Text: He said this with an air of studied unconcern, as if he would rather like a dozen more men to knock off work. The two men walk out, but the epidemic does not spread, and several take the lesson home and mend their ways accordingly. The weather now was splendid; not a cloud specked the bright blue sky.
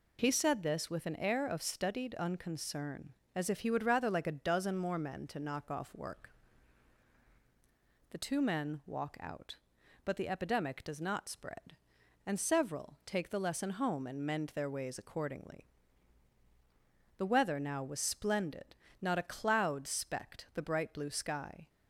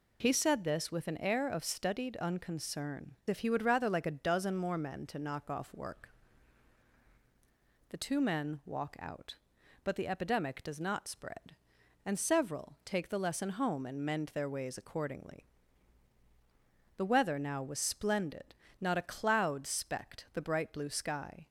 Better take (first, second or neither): first